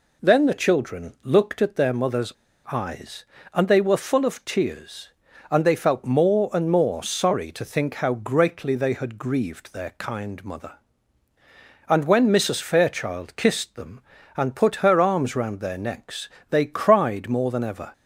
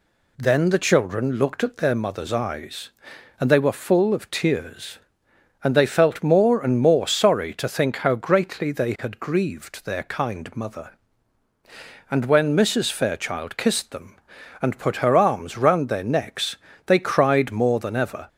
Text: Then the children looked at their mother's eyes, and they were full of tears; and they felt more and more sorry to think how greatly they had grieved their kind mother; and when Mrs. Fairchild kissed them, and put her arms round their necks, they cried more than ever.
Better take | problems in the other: second | pauses between "mother's" and "eyes"; at 2.3 s; 0.38 s long

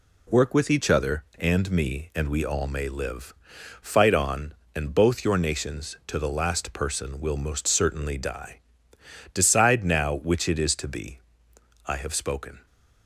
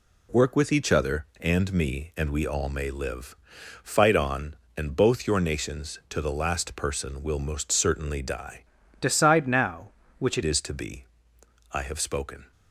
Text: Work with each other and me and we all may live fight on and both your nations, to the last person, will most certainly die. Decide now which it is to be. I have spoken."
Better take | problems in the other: first | pauses between "live" and "fight"; noticeable; at 3.3 s; 0.46 s long; noticeable in the first // changes voice from "Decide" to "it"; from 8.9 to 10.4 s; 1.5 s long

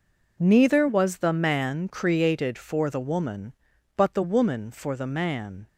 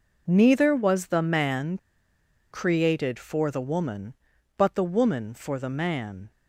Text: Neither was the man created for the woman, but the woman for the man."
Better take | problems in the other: first | pauses between "man" and "created"; noticeable; at 1.7 s; 0.74 s long

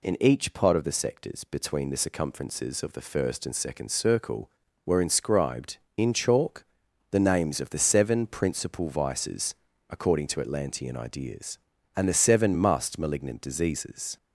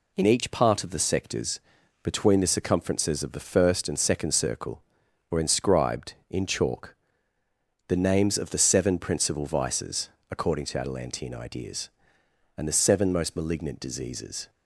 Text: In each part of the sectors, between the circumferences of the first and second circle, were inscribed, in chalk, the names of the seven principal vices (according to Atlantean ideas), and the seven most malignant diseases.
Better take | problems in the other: second | says "must" for "most"; at 12.5 s

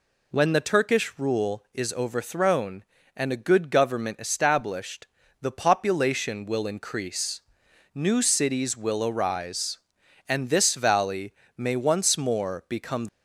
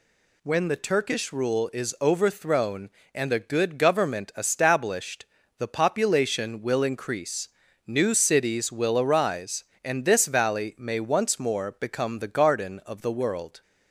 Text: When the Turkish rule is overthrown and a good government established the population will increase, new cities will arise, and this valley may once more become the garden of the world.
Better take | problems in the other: second | pauses between "established" and "the"; slight; at 5.0 s; 0.36 s long; slight in the second // pauses between "valley" and "may"; slight; at 11.3 s; 0.24 s long // stops before "the garden of the world"; at 13.0 s

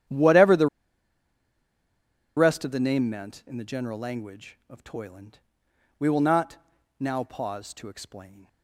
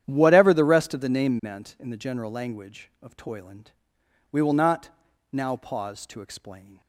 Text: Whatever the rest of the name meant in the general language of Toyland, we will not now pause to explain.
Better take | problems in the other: second | starts louder than the rest; strong; until 2.7 s; 10 dB; strong in the second // pauses between "the" and "rest"; strong; at 0.6 s; 1.6 s long // pauses between "not" and "now"; at 6.5 s; 0.44 s long; also in the second

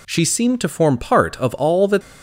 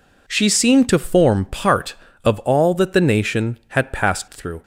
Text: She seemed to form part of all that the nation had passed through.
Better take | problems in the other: second | stops before "the nation had passed through"; at 2.0 s

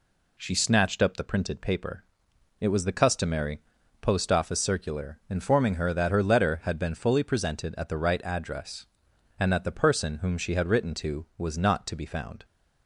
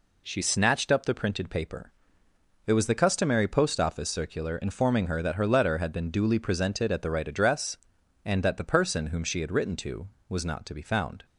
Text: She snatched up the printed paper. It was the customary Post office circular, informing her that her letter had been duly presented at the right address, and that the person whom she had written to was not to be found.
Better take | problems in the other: second | pauses between "customary" and "Post"; at 3.5 s; 0.40 s long // says "fully" for "duly"; at 6.9 s

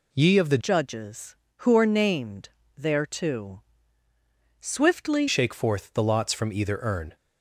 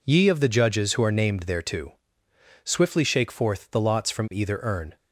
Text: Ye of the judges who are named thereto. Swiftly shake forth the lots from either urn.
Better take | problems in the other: second | changes voice from "judges" to "Swiftly"; from 0.5 to 5.2 s; 4.7 s long // pauses between "named" and "thereto"; slight; at 2.4 s; 0.30 s long

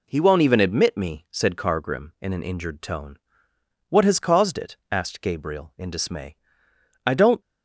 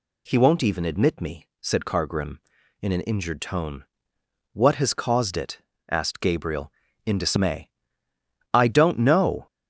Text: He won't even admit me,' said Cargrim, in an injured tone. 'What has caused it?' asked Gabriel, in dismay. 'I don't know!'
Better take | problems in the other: second | stops before "know"; at 7.4 s

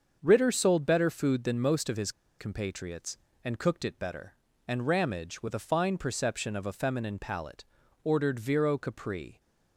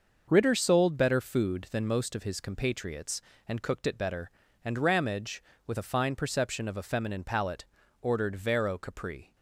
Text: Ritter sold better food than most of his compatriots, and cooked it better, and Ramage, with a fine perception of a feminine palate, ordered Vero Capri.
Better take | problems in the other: second | starts louder than the rest; until 1.2 s; 6.5 dB; noticeable in the second // pauses between "his" and "compatriots"; slight; at 2.0 s; 0.29 s long

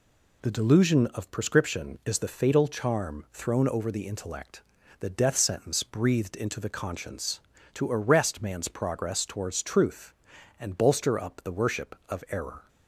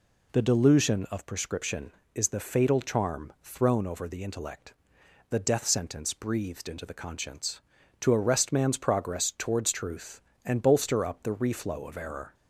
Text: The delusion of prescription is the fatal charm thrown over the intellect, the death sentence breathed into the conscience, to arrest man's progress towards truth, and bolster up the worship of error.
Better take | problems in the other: first | says "reflow" for "worship"; at 11.3 s

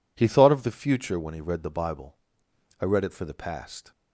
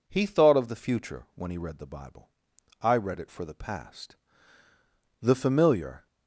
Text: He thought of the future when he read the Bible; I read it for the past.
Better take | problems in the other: first | goes on to say "The familiar"; noticeable; from 5.2 s on; 0.86 s long

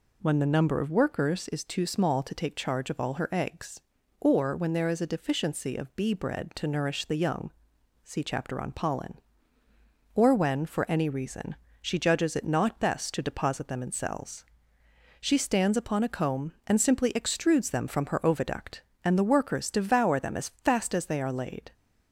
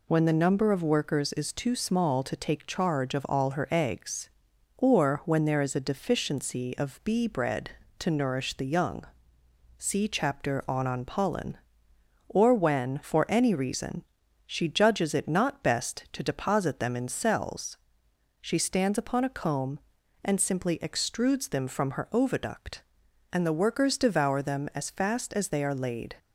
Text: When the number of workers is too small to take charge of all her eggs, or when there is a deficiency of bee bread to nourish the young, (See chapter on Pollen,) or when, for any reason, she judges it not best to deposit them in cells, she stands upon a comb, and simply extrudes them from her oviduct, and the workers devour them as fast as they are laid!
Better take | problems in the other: first | says "on" twice; at 10.8 s

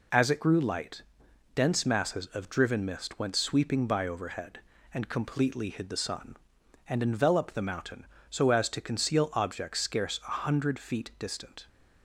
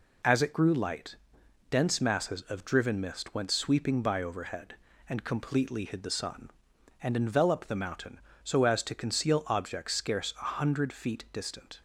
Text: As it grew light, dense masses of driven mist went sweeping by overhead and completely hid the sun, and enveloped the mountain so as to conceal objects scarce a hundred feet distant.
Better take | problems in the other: neither | none

